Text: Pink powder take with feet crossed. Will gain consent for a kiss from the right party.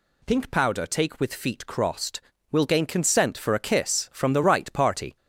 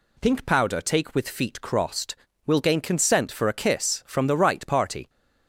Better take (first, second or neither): second